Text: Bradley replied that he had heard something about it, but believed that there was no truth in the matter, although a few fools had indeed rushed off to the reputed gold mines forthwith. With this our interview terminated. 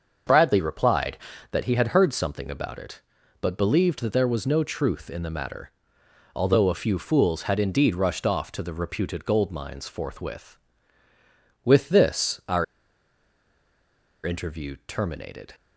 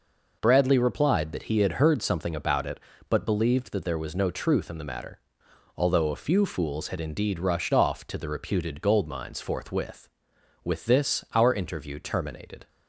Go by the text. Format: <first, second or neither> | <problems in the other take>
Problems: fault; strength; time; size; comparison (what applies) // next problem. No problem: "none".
second | starts louder than the rest; until 1.6 s; 6.5 dB // pauses between "our" and "interview"; strong; at 12.6 s; 1.6 s long